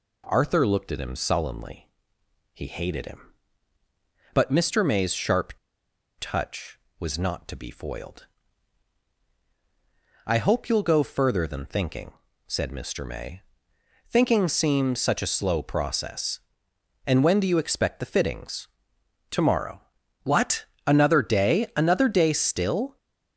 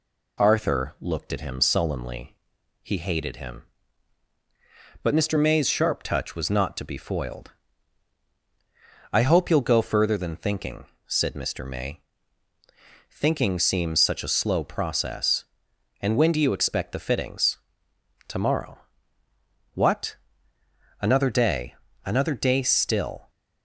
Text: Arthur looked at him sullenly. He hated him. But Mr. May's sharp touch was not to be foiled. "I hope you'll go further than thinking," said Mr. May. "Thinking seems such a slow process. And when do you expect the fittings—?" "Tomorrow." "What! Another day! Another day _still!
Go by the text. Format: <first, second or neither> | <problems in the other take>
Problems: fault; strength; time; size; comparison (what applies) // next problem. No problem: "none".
second | pauses between "sharp" and "touch"; noticeable; at 5.5 s; 0.68 s long